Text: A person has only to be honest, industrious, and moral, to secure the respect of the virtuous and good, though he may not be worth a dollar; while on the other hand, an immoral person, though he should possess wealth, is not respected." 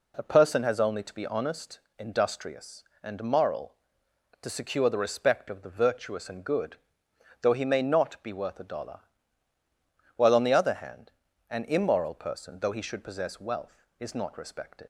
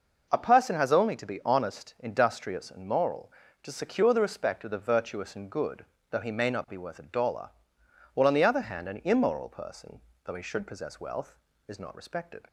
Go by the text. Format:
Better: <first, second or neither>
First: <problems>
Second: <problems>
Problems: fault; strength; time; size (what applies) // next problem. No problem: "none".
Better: second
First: leaves "respected" unfinished; at 14.8 s; 80 ms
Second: none